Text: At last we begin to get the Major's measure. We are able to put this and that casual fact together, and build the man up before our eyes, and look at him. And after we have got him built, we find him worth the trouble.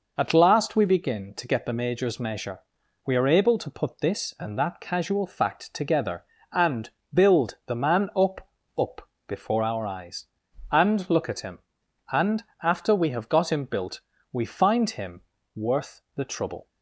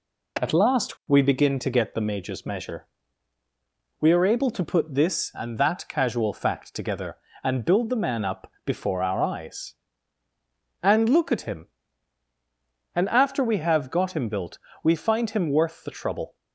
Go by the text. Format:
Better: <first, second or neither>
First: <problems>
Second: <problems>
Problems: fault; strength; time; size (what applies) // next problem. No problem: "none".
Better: second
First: pauses between "and" and "build"; slight; at 6.8 s; 0.24 s long // says "up" twice; at 8.7 s // pauses between "And" and "after"; slight; at 12.4 s; 0.18 s long // pauses between "him" and "worth"; slight; at 15.2 s; 0.34 s long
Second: none